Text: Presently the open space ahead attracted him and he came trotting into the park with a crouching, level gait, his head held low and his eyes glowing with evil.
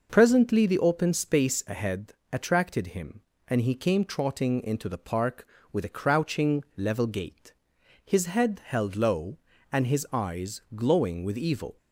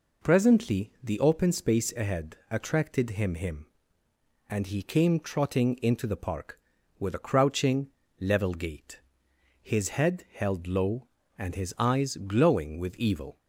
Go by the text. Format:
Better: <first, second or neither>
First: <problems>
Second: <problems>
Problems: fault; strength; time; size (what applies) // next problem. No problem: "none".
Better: first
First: pauses between "ahead" and "attracted"; slight; at 2.1 s; 0.18 s long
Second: pauses between "ahead" and "attracted"; slight; at 2.3 s; 0.16 s long // says "him" twice; at 3.3 s